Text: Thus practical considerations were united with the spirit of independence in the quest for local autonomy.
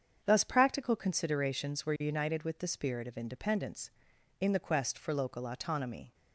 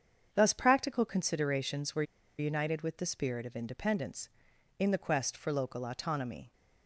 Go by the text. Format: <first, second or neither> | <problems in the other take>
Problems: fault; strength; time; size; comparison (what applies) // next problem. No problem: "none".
first | starts louder than the rest; strong; until 1.3 s; 7.5 dB; strong in the first // pauses between "were" and "united"; slight; at 2.0 s; 0.35 s long